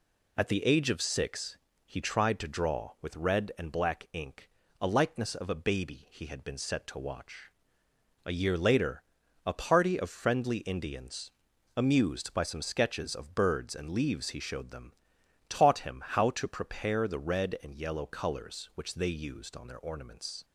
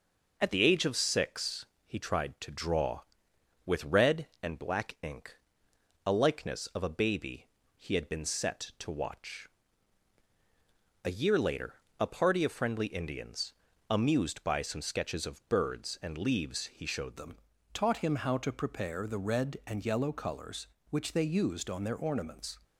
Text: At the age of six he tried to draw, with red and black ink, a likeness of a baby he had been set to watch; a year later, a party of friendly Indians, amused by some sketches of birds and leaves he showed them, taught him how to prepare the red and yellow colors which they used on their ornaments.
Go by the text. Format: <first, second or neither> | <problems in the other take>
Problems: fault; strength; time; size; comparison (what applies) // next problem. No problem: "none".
first | pauses between "six" and "he"; slight; at 1.6 s; 0.22 s long; slight in the first // pauses between "baby" and "he"; slight; at 7.4 s; 0.28 s long // changes voice at "them"; from 17.1 s on; 5.4 s long